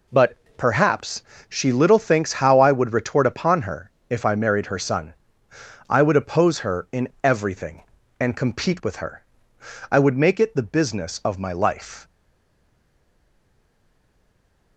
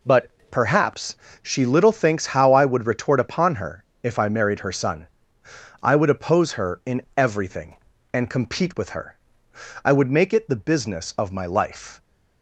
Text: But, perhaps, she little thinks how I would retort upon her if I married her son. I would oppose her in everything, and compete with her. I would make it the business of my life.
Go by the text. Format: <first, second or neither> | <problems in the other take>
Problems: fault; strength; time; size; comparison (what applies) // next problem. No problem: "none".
second | pauses between "her" and "if"; slight; at 3.8 s; 0.18 s long; slight in the second // stays silent after the last word; strong; from 12.0 s on; 2.7 s long